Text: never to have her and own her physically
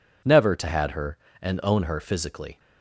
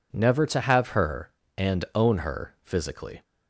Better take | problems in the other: second | says "had" for "have"; at 0.6 s

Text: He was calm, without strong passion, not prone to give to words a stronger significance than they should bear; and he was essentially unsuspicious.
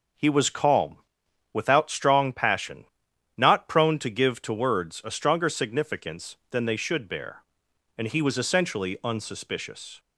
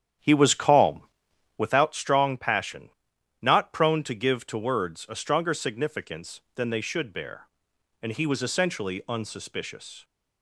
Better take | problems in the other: first | starts louder than the rest; strong; until 1.8 s; 9 dB

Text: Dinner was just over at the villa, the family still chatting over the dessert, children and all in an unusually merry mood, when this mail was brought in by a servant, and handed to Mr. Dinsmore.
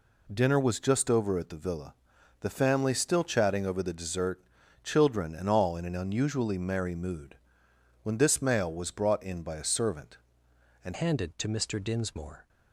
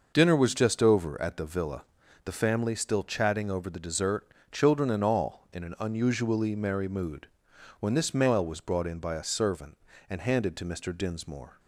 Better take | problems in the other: second | changes voice at "handed"; from 10.9 s on; 1.5 s long

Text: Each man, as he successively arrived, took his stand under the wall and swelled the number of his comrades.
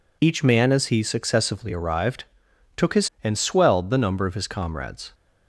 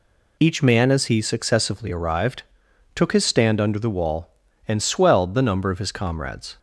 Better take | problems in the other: second | skips "stand under the wall"; at 3.1 s

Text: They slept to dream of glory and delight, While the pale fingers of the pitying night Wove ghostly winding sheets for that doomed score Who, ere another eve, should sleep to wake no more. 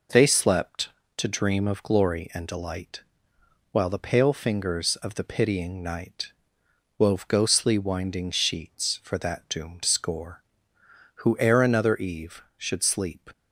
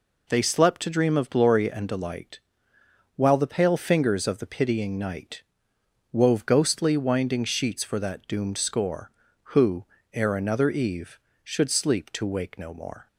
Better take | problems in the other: second | pauses between "night" and "Wove"; noticeable; at 6.3 s; 0.66 s long; noticeable in the second // stops before "to wake no more"; at 13.3 s

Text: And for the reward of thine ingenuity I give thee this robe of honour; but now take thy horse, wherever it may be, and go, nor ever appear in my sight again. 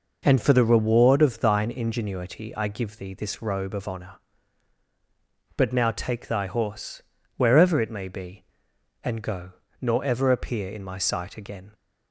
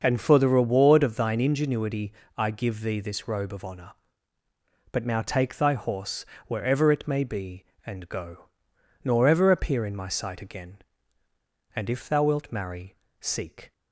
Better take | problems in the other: first | starts louder than the rest; until 1.0 s; 6.5 dB // pauses between "ingenuity" and "I"; slight; at 2.1 s; 0.24 s long // goes on to say "And if thou wilt marry seek"; strong; from 11.7 s on; 1.9 s long

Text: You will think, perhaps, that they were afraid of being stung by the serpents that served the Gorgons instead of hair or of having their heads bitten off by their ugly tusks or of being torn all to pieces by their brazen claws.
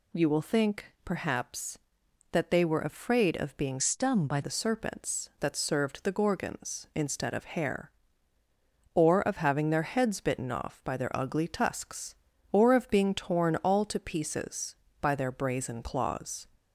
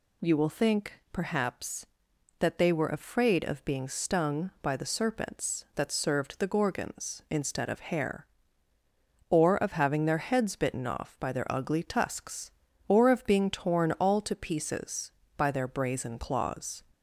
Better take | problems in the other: second | changes voice from "stung" to "by"; from 3.7 to 4.3 s; 0.6 s long

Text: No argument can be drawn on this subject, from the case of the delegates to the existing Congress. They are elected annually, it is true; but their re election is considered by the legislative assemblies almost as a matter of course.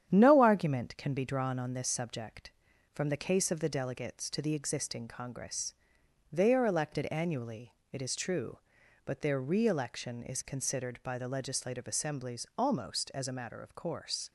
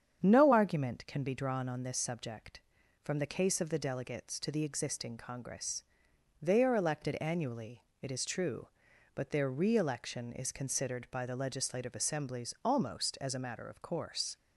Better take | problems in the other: second | gets quieter; throughout; 3.5 dB // starts louder than the rest; strong; until 1.1 s; 9.5 dB; strong in the second

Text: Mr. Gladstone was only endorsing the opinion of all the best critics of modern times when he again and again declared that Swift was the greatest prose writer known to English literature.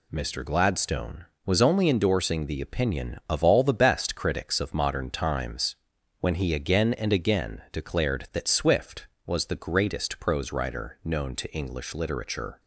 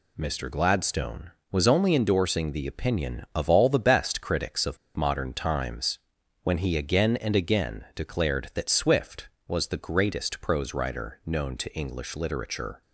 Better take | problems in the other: first | pauses between "of" and "modern"; slight; at 4.7 s; 0.18 s long // pauses between "times" and "when"; noticeable; at 5.9 s; 0.46 s long; noticeable in the first

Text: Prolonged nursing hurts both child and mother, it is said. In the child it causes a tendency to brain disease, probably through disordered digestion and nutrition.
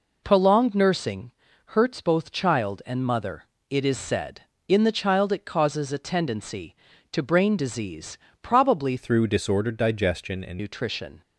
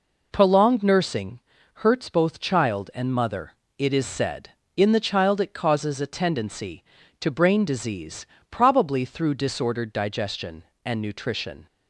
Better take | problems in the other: second | pauses between "nursing" and "hurts"; slight; at 1.3 s; 0.34 s long; slight in the second // changes voice from "through" to "and"; from 8.9 to 10.5 s; 1.6 s long

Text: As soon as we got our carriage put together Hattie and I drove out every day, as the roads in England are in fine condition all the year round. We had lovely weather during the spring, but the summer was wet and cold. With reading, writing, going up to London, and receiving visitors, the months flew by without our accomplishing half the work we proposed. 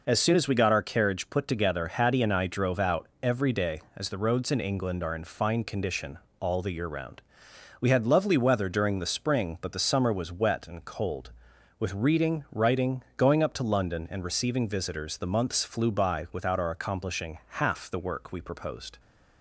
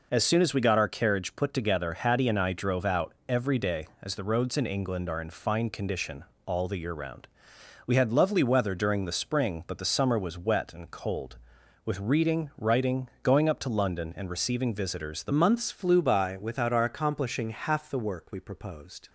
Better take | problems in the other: first | pauses between "condition" and "all"; slight; at 6.2 s; 0.22 s long; slight in the first // changes voice at "months"; from 15.3 s on; 3.7 s long

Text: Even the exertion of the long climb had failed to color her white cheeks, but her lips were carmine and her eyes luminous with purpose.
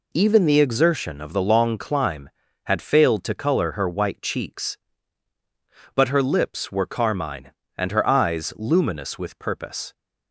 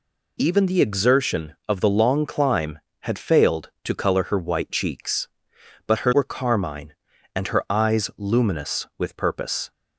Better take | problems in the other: first | skips "lips"; at 6.1 s

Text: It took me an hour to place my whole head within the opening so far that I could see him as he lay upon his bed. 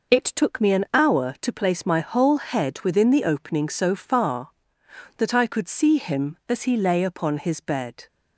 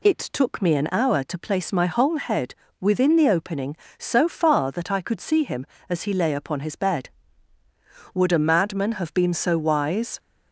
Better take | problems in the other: first | pauses between "head" and "within"; slight; at 2.5 s; 0.26 s long // goes on to say "would a madman have been so wise"; strong; from 8.1 s on; 2.0 s long

